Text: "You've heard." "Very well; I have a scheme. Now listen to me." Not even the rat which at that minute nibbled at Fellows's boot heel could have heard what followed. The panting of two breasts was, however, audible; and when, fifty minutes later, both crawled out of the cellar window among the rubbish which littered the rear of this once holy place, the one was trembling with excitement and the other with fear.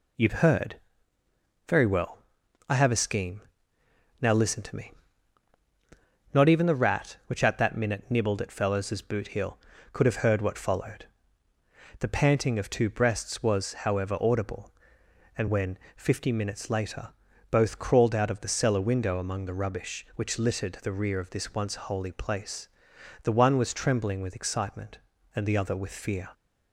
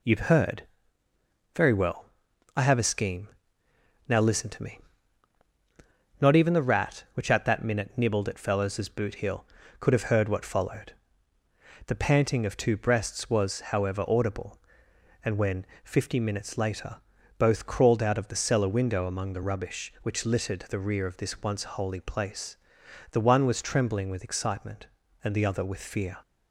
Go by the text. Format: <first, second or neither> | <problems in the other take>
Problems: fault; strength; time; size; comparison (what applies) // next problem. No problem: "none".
neither | none